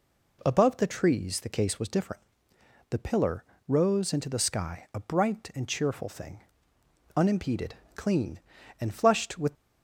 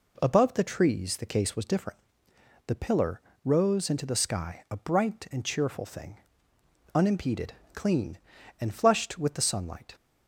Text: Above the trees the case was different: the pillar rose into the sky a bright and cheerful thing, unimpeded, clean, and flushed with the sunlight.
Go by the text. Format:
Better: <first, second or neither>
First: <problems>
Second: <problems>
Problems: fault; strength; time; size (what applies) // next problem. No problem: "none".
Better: second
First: pauses between "pillar" and "rose"; slight; at 3.4 s; 0.24 s long // stops before "the sunlight"; at 9.5 s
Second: pauses between "pillar" and "rose"; slight; at 3.1 s; 0.24 s long